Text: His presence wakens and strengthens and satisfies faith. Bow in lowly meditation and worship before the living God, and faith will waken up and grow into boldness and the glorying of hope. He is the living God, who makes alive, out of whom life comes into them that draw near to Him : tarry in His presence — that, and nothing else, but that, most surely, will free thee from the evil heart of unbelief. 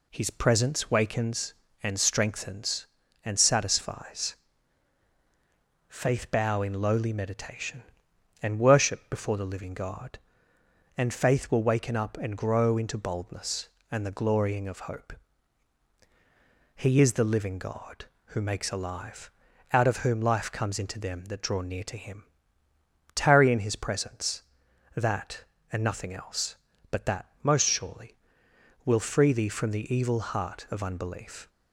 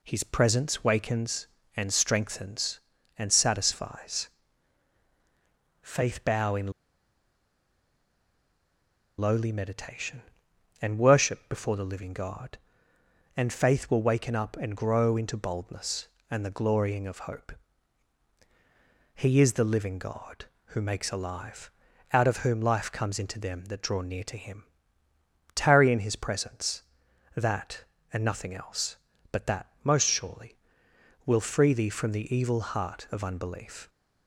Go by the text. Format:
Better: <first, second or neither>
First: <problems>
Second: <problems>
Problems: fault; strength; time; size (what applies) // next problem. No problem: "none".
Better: first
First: pauses between "satisfies" and "faith"; strong; at 4.3 s; 1.5 s long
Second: pauses between "satisfies" and "faith"; strong; at 4.2 s; 1.5 s long // pauses between "in" and "lowly"; strong; at 6.7 s; 2.4 s long